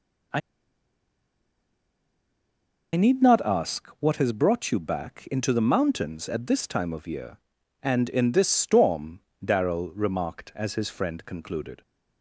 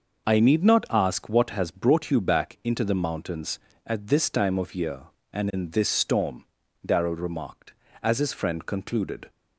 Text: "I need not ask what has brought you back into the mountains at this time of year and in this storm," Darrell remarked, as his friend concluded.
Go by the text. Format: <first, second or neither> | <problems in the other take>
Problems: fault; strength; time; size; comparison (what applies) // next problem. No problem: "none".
second | pauses between "I" and "need"; strong; at 0.4 s; 2.5 s long